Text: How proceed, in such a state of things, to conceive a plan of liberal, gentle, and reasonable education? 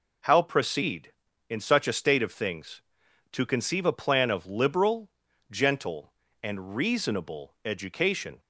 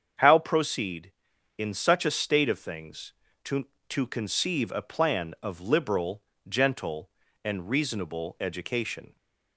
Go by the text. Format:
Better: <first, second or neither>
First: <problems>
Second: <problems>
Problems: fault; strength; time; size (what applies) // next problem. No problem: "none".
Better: first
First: none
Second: starts louder than the rest; strong; until 1.6 s; 7.5 dB // says "to" twice; at 3.8 s